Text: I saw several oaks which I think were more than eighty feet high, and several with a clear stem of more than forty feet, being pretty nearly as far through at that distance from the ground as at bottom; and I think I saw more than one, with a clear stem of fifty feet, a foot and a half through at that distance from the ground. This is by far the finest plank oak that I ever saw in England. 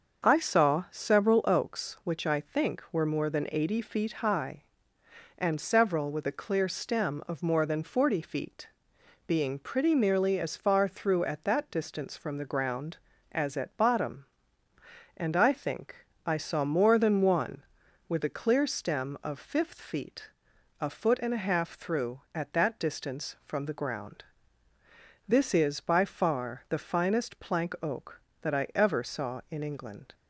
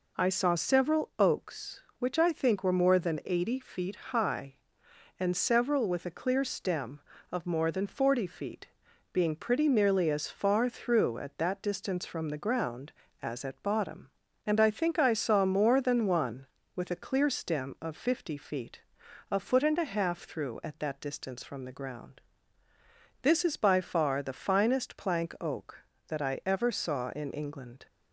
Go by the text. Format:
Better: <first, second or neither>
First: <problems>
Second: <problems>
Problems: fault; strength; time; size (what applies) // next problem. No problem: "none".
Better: second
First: starts louder than the rest; until 1.3 s; 6.5 dB // pauses between "think" and "I"; slight; at 15.9 s; 0.32 s long // says "fifth" for "fifty"; at 19.3 s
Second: none